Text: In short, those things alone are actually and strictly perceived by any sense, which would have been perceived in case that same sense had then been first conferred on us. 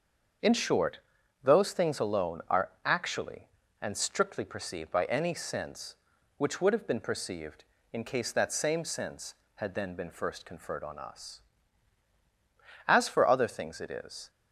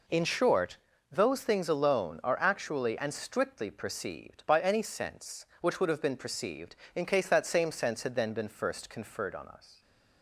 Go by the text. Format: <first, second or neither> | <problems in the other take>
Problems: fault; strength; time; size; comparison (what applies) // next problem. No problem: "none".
second | starts louder than the rest; until 1.8 s; 7 dB // pauses between "are" and "actually"; slight; at 2.6 s; 0.16 s long // goes on to say "As for other things it is"; from 12.8 s on; 1.4 s long